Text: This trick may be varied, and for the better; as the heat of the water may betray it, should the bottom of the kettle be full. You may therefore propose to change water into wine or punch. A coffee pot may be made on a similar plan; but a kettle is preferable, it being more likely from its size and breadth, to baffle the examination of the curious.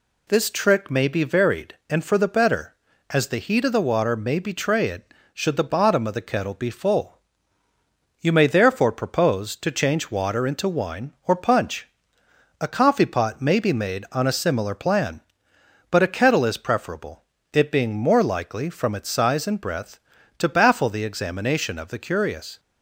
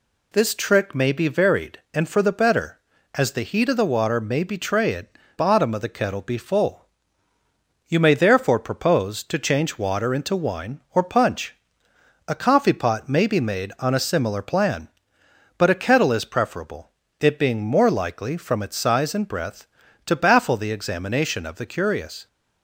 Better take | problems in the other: first | skips "should the"; at 5.2 s

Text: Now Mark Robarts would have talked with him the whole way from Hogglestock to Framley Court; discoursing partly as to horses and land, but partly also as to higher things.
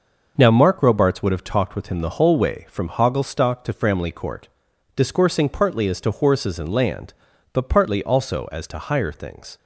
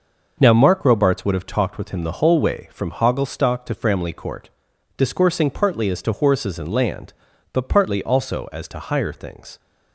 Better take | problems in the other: neither | starts louder than the rest; noticeable; the same in both

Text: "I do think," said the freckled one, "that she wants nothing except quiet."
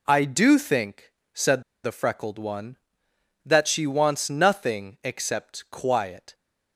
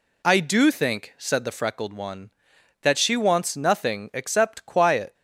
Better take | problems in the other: second | pauses between "said" and "the"; slight; at 1.6 s; 0.21 s long

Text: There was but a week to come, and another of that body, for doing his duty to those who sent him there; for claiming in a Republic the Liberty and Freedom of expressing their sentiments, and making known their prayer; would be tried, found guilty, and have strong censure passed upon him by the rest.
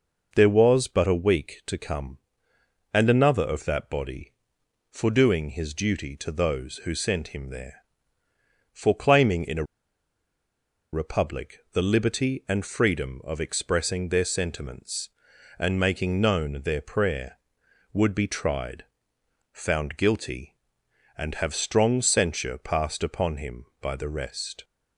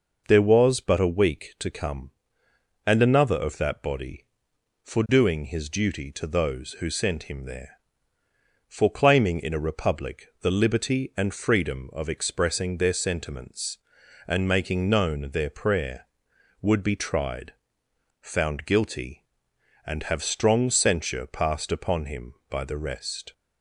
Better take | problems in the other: second | pauses between "a" and "Republic"; strong; at 9.6 s; 1.2 s long

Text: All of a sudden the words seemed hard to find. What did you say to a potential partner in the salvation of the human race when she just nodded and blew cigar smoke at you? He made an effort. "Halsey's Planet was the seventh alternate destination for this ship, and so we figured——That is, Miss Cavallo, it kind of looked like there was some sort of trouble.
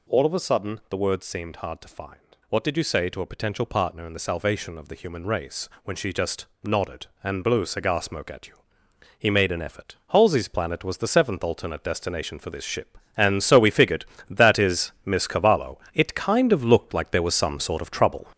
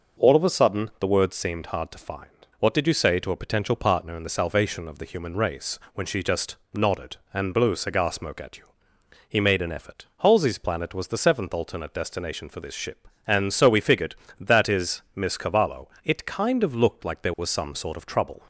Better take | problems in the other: second | gets louder; noticeable; throughout; 5.5 dB // pauses between "race" and "when"; slight; at 5.6 s; 0.16 s long; slight in the second // pauses between "just" and "nodded"; slight; at 6.4 s; 0.18 s long; slight in the second

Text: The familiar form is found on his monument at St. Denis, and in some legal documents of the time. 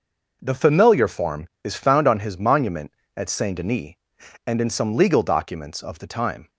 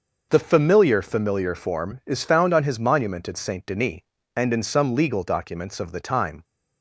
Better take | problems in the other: first | starts louder than the rest; noticeable; until 1.3 s; 6 dB // says "familiar" twice; at 1.0 s

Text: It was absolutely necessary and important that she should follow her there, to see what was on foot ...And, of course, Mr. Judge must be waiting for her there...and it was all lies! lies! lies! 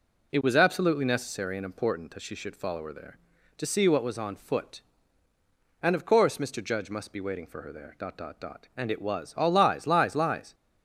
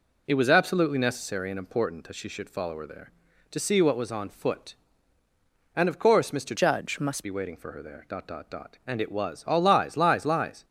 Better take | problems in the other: first | changes voice from "Judge" to "must"; from 6.5 to 7.2 s; 0.7 s long

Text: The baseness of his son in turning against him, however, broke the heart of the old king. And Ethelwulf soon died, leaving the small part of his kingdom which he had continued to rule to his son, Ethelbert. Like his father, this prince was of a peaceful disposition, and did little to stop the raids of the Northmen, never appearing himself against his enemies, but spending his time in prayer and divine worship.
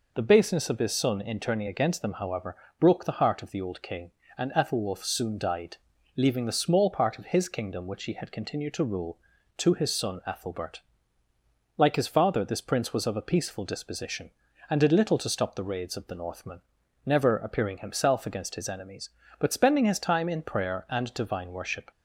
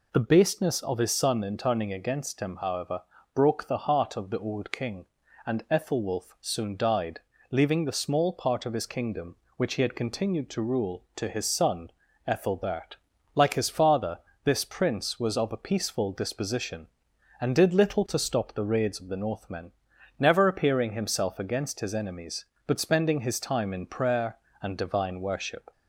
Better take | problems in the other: second | says "them" for "him"; at 2.0 s

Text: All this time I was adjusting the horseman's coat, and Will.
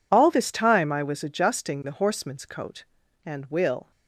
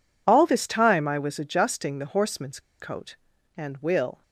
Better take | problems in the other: first | pauses between "horseman's" and "coat"; slight; at 2.5 s; 0.20 s long

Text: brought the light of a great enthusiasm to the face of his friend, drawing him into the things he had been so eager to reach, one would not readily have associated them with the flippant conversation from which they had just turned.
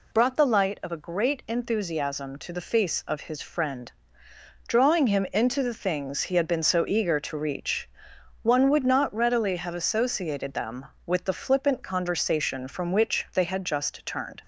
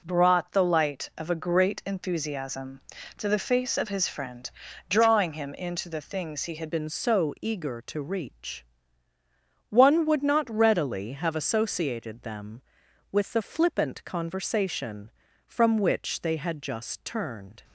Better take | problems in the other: first | changes voice at "been"; from 6.7 s on; 10.9 s long

